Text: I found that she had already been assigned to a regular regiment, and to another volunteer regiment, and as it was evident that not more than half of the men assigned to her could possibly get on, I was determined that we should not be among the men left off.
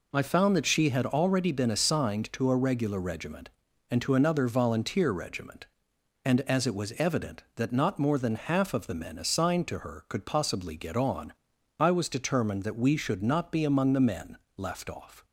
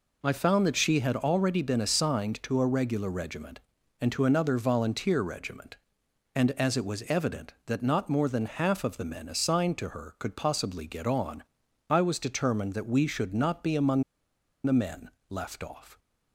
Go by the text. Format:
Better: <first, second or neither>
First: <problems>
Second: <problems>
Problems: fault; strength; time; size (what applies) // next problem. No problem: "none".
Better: first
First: pauses between "men" and "left"; slight; at 14.3 s; 0.18 s long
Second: pauses between "among" and "the"; noticeable; at 14.0 s; 0.61 s long // pauses between "men" and "left"; slight; at 15.1 s; 0.18 s long